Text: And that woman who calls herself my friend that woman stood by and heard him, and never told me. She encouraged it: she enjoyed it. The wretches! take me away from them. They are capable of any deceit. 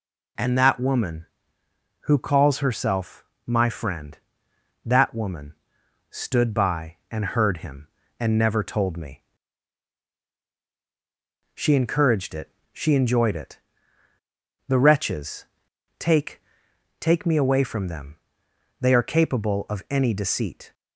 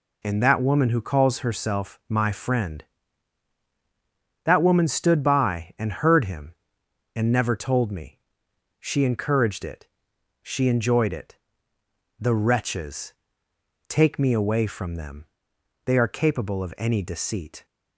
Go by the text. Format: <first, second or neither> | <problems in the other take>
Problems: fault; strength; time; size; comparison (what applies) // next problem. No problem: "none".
second | pauses between "herself" and "my"; slight; at 3.2 s; 0.22 s long // pauses between "woman" and "stood"; noticeable; at 5.5 s; 0.58 s long // says "take" twice; at 16.9 s